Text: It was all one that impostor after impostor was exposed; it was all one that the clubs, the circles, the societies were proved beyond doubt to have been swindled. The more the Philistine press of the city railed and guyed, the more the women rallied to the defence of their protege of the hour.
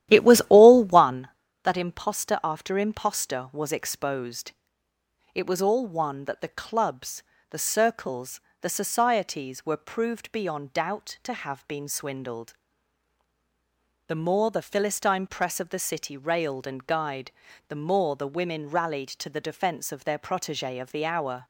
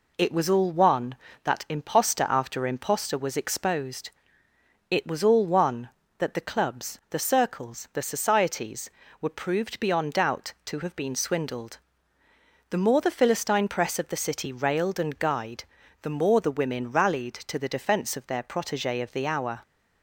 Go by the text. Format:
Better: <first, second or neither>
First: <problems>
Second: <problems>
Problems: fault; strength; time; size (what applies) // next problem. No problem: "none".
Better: second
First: starts louder than the rest; strong; until 1.2 s; 12.5 dB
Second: none